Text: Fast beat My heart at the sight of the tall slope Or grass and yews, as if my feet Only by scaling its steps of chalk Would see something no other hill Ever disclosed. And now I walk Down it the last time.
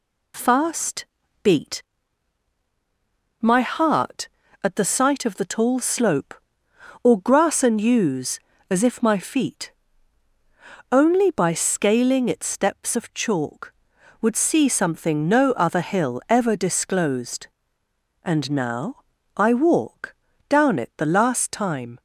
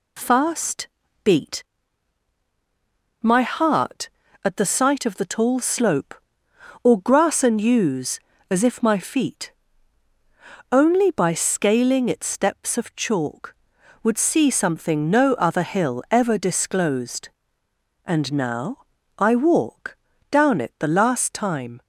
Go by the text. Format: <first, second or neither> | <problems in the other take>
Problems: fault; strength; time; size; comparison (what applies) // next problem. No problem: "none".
neither | pauses between "Fast" and "beat"; the same in both // pauses between "beat" and "My"; strong; the same in both // pauses between "feet" and "Only"; the same in both // pauses between "now" and "I"; the same in both // pauses between "walk" and "Down"; slight; the same in both